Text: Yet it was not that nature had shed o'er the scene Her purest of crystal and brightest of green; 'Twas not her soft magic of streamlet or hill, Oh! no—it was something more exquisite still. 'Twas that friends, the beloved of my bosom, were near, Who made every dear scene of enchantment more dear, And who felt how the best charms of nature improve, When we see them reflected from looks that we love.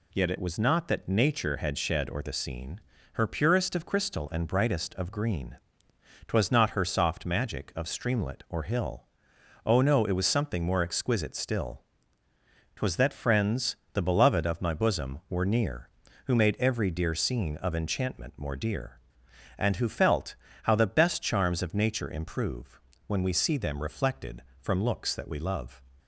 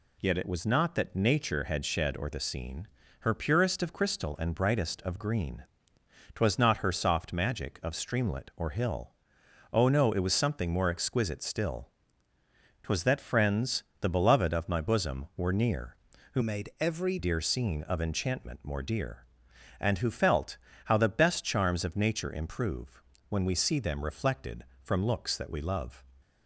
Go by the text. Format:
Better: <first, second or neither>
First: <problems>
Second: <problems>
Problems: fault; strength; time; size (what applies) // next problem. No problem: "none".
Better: first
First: pauses between "scene" and "Her"; slight; at 2.8 s; 0.34 s long // pauses between "felt" and "how"; slight; at 20.3 s; 0.28 s long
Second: pauses between "scene" and "Her"; slight; at 2.8 s; 0.34 s long // changes voice from "made" to "every"; from 16.4 to 17.1 s; 0.7 s long // pauses between "felt" and "how"; slight; at 20.5 s; 0.28 s long